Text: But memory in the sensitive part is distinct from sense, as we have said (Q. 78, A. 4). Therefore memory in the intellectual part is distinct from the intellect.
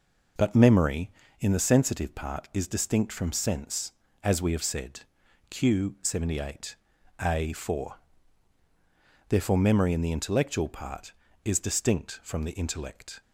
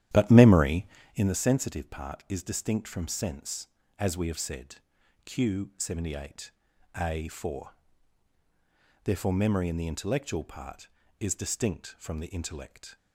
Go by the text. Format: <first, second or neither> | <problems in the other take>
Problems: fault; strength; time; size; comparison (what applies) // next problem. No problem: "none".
first | starts louder than the rest; strong; until 1.4 s; 11.5 dB